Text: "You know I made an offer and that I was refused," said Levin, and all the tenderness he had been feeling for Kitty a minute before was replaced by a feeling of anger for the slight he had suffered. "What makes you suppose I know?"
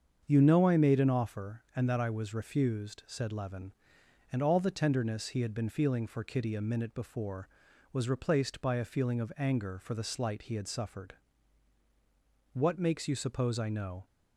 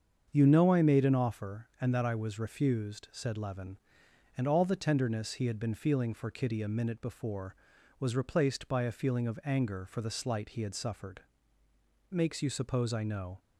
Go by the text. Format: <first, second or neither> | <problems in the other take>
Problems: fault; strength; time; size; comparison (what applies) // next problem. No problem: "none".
first | starts louder than the rest; strong; until 1.3 s; 7 dB; strong in the first // skips "What"; at 11.6 s